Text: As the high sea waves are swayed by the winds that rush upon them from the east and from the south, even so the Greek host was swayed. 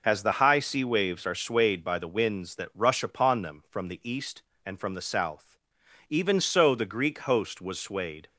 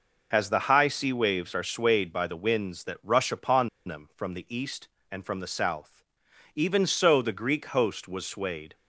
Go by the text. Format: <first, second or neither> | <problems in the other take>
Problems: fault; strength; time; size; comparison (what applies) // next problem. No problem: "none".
first | pauses between "upon" and "them"; slight; at 3.6 s; 0.17 s long